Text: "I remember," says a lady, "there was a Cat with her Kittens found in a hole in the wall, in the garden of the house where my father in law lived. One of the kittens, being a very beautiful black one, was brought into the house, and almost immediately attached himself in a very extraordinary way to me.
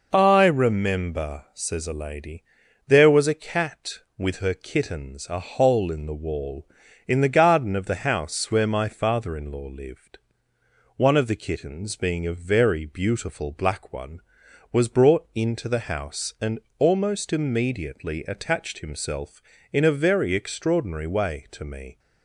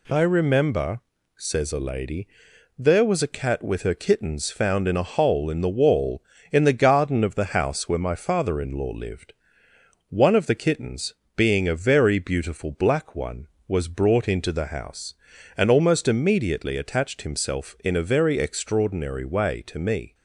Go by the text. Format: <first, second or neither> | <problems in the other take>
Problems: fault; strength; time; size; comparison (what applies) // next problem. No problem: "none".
second | skips "found in"; at 5.2 s // pauses between "and" and "almost"; slight; at 16.5 s; 0.20 s long